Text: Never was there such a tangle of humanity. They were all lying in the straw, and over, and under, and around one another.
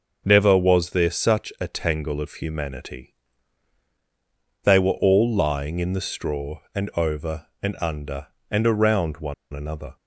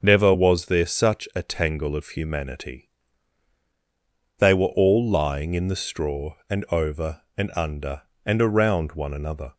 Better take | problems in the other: second | starts louder than the rest; until 1.2 s; 6 dB; also in the second // pauses between "one" and "another"; slight; at 9.3 s; 0.19 s long

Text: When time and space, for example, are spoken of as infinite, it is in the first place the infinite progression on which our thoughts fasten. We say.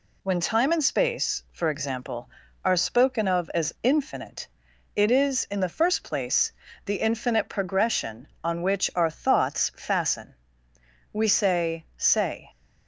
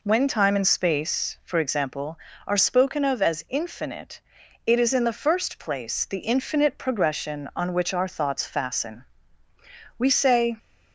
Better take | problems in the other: second | pauses between "place" and "the"; slight; at 6.5 s; 0.32 s long // says "say" twice; at 11.9 s

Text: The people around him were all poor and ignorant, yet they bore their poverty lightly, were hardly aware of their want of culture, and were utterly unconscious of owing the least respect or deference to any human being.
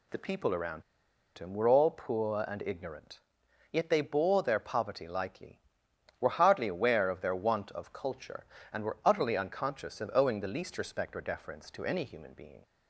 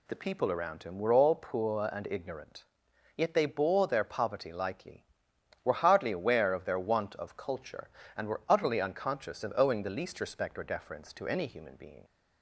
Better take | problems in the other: second | pauses between "around" and "him"; noticeable; at 0.8 s; 0.55 s long

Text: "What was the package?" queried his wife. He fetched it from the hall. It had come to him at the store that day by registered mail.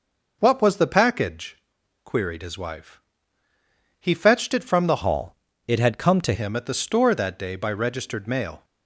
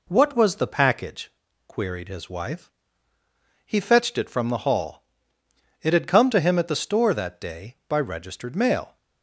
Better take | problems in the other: second | changes voice from "hall" to "to"; from 5.0 to 6.3 s; 1.3 s long

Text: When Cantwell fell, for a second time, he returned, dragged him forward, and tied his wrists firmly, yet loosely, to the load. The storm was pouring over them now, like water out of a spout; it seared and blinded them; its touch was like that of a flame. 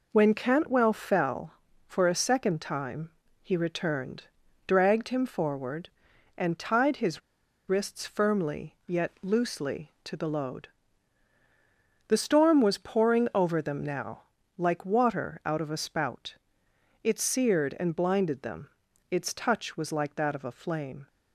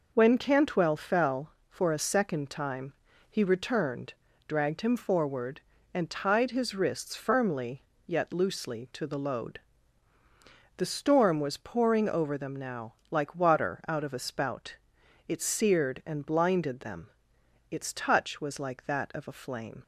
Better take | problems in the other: second | pauses between "his" and "wrists"; noticeable; at 7.2 s; 0.48 s long

